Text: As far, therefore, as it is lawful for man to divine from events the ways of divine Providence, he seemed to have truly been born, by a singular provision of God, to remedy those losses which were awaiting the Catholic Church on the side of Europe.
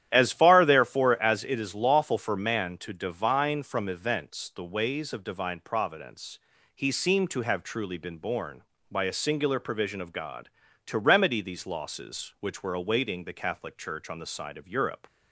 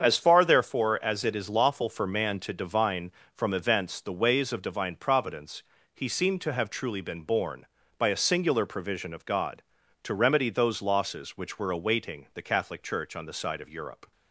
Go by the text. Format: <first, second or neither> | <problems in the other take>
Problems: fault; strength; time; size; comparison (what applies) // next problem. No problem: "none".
second | starts louder than the rest; strong; until 1.1 s; 11 dB; strong in the second // says "these" for "those"; at 11.4 s